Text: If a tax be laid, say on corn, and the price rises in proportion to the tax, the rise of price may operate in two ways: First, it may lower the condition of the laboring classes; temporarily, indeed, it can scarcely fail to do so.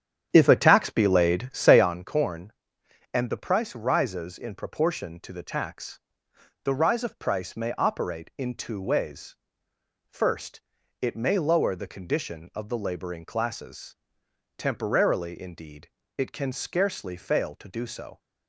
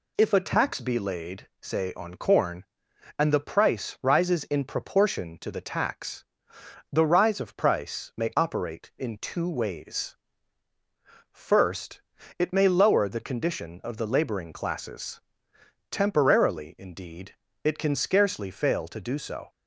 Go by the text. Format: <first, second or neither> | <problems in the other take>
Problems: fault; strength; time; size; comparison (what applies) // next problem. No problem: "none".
second | starts louder than the rest; strong; until 1.9 s; 9.5 dB